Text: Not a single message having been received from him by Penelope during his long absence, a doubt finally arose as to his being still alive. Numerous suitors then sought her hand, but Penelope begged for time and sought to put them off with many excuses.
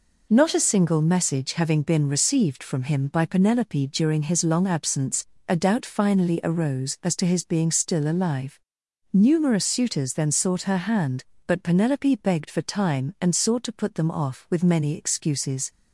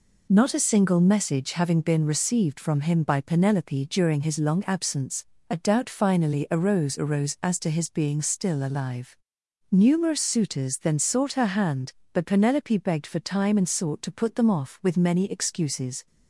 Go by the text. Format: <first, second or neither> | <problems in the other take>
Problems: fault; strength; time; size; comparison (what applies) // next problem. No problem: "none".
first | says "arose" twice; at 6.9 s